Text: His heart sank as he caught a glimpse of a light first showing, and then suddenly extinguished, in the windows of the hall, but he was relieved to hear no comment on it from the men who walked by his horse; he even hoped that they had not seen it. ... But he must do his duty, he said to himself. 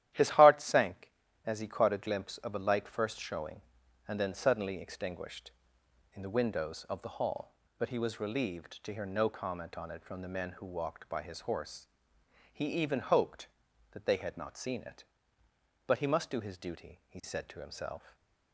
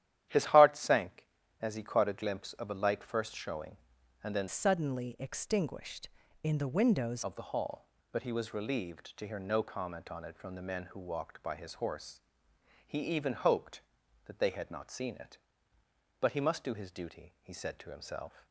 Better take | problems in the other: first | starts louder than the rest; strong; until 1.6 s; 12 dB; strong in the first // changes voice from "suddenly" to "windows"; from 4.4 to 7.2 s; 2.8 s long

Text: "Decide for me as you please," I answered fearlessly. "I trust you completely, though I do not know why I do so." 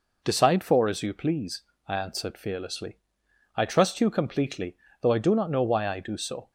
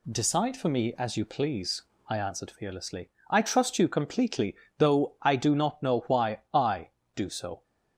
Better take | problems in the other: second | skips "me"; at 0.8 s

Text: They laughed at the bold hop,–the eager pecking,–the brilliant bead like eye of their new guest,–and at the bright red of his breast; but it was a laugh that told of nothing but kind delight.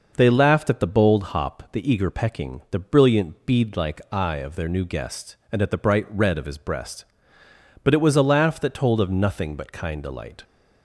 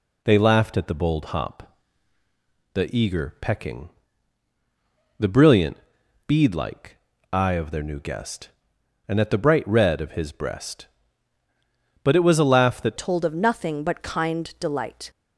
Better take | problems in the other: first | pauses between "brilliant" and "bead"; noticeable; at 5.7 s; 0.50 s long // pauses between "like" and "eye"; slight; at 6.9 s; 0.34 s long // changes voice at "told"; from 12.9 s on; 2.1 s long

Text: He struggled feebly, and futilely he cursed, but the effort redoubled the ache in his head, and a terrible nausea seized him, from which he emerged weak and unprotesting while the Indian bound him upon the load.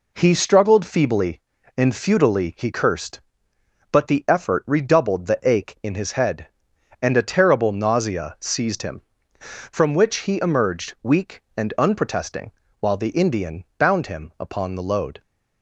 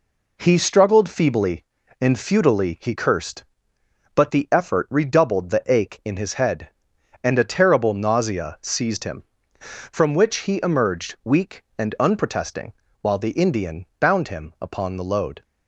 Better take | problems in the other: neither | pauses between "unprotesting" and "while"; slight; the same in both

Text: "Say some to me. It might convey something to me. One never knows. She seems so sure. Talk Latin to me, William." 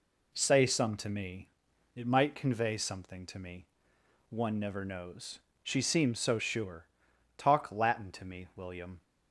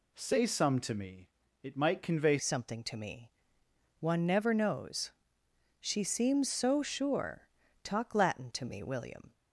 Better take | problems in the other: first | changes voice at "something"; from 2.3 s on; 7.0 s long

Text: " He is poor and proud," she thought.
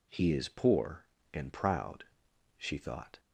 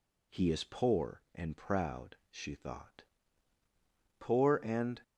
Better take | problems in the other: first | goes on to say "Poor and"; noticeable; from 4.2 s on; 0.80 s long

